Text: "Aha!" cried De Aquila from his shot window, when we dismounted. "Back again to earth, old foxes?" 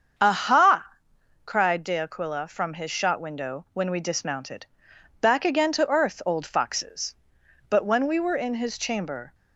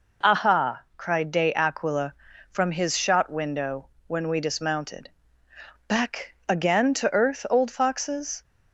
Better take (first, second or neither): second